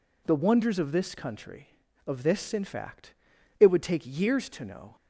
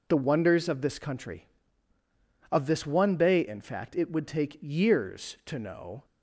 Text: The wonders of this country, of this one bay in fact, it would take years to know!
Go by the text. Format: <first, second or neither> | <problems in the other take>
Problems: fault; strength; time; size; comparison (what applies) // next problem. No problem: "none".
second | skips "one bay"; at 2.5 s